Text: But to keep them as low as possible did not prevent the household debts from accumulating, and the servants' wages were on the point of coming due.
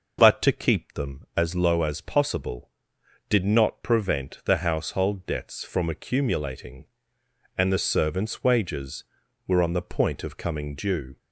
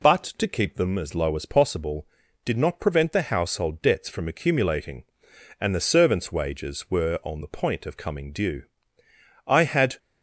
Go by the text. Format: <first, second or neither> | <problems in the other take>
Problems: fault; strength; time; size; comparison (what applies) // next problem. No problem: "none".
first | goes on to say "I had"; from 9.4 s on; 0.51 s long